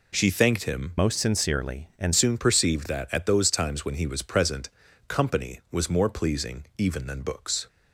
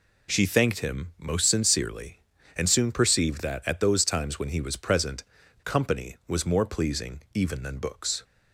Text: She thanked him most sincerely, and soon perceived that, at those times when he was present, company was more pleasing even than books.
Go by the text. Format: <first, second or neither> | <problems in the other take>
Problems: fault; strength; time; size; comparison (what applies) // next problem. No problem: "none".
second | changes voice from "most" to "and"; from 0.9 to 2.1 s; 1.2 s long